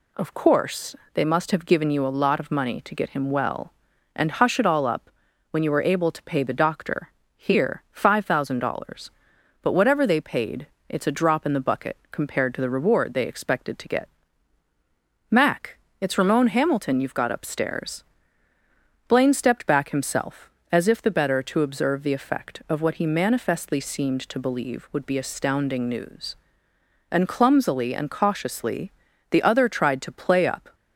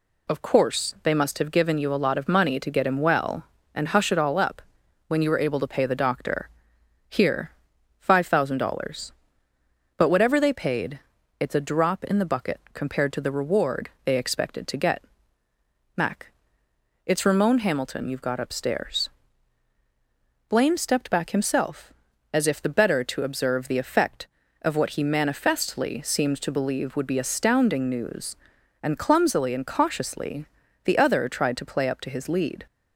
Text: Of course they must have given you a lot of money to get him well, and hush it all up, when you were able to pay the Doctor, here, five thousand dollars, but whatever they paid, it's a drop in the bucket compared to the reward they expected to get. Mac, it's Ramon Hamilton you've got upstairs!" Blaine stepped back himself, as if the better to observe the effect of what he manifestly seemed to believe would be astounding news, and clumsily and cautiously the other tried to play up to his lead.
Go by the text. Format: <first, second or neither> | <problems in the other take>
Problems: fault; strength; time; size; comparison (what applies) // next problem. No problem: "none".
second | pauses between "course" and "they"; slight; at 0.9 s; 0.18 s long // pauses between "cautiously" and "the"; at 28.9 s; 0.40 s long; also in the second // stops before "to his lead"; at 30.7 s